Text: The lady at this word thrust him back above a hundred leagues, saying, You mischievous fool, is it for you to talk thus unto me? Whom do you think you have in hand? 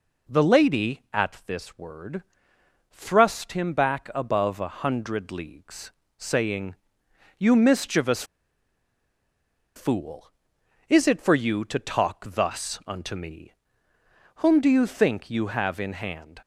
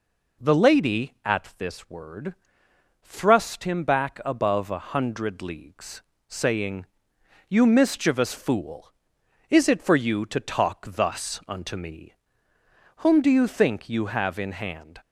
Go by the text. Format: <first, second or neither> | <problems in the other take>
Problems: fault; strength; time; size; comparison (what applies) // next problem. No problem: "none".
second | pauses between "word" and "thrust"; noticeable; at 2.2 s; 0.70 s long; noticeable in the second // pauses between "mischievous" and "fool"; strong; at 8.2 s; 1.5 s long